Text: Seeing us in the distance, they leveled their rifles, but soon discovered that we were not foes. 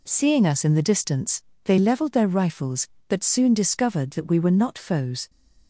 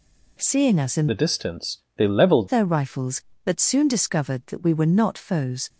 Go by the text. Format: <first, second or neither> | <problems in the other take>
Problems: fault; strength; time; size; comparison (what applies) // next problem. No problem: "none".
first | changes voice from "the" to "leveled"; from 1.0 to 2.4 s; 1.4 s long